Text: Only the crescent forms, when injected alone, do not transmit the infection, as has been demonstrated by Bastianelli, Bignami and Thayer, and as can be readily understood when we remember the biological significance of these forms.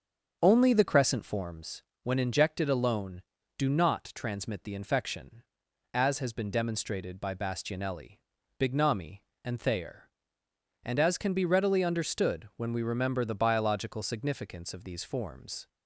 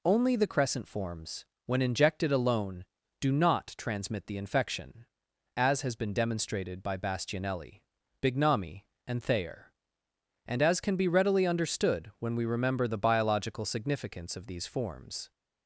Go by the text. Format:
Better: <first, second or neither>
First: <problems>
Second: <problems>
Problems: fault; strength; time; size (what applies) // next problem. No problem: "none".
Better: second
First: starts louder than the rest; until 1.4 s; 7 dB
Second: none